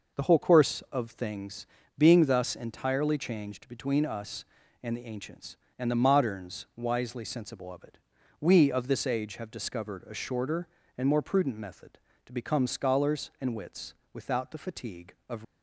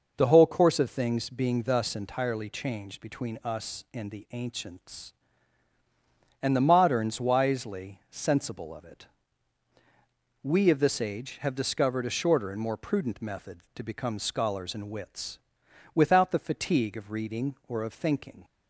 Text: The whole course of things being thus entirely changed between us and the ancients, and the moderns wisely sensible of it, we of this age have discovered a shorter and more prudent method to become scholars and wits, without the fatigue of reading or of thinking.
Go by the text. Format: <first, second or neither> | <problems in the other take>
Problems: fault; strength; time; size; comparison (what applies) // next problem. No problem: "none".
second | pauses between "things" and "being"; slight; at 1.6 s; 0.32 s long // stops before "reading or of thinking"; at 15.4 s